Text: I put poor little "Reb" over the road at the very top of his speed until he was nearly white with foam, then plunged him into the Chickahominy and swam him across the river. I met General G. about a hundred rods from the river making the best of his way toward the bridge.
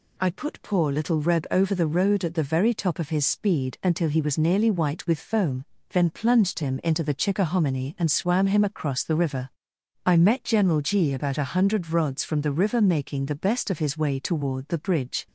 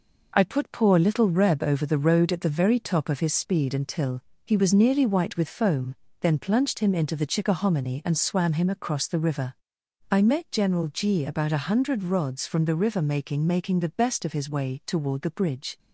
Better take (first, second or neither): first